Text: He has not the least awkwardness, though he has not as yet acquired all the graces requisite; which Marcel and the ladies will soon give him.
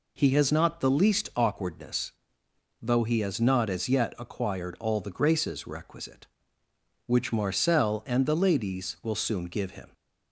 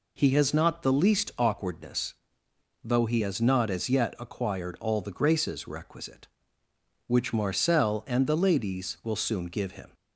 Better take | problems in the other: neither | none

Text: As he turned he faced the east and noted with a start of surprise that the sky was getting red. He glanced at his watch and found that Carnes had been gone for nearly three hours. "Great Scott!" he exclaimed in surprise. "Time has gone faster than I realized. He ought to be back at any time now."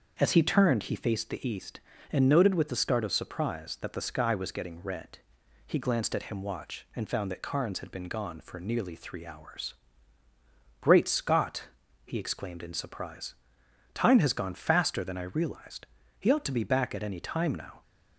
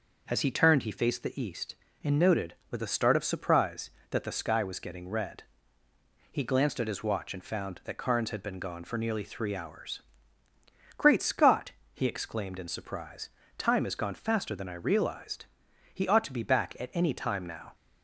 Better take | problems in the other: second | starts louder than the rest; until 1.2 s; 6.5 dB // says "him" for "his"; at 6.2 s

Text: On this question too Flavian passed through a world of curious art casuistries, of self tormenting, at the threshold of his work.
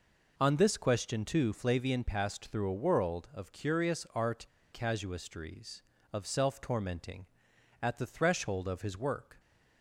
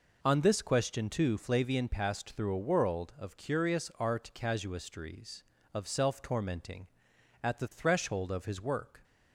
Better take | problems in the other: second | pauses between "art" and "casuistries"; slight; at 4.4 s; 0.29 s long

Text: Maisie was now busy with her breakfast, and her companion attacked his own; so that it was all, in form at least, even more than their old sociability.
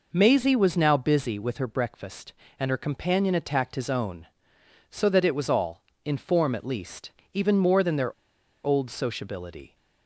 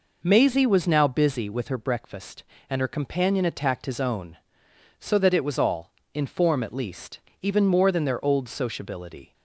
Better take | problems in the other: second | pauses between "their" and "old"; noticeable; at 8.1 s; 0.51 s long

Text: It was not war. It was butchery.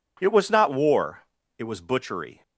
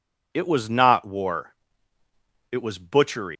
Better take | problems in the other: first | leaves "butchery" unfinished; at 3.3 s; 165 ms

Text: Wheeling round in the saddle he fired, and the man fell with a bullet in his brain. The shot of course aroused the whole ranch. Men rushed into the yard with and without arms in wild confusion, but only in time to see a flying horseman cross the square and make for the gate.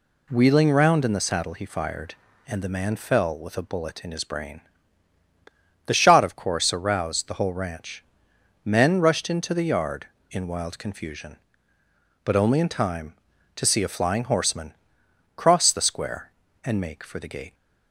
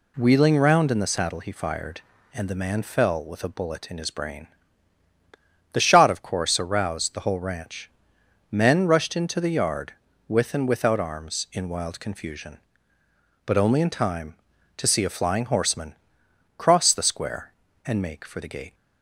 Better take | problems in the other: second | skips "with and without arms"; at 10.1 s // pauses between "horseman" and "cross"; noticeable; at 14.7 s; 0.62 s long; noticeable in the second

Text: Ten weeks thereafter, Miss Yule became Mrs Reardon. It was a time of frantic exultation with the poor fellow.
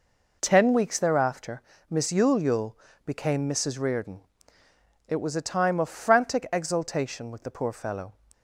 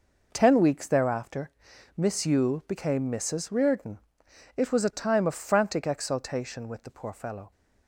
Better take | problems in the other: second | says "Yule" twice; at 2.4 s

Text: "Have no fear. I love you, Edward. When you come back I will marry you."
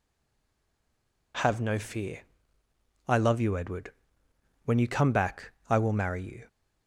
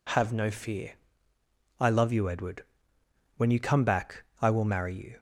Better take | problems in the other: second | stays silent before the first word; noticeable; until 1.3 s; 1.3 s long // pauses between "back" and "I"; slight; at 5.5 s; 0.16 s long; slight in the second

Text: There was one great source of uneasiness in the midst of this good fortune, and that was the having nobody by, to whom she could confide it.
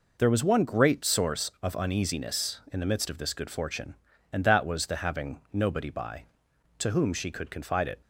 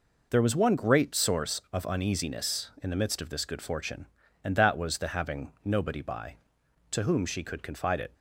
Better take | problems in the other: neither | none

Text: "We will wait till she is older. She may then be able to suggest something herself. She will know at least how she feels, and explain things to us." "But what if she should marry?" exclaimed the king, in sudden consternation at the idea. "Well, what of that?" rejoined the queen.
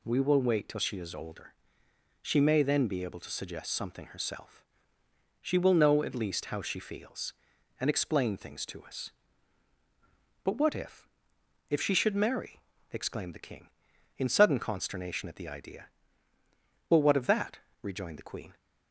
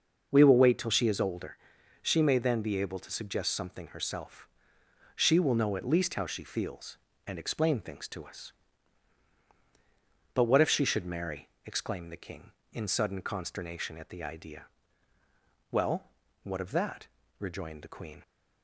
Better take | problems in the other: second | says "if" twice; at 11.6 s

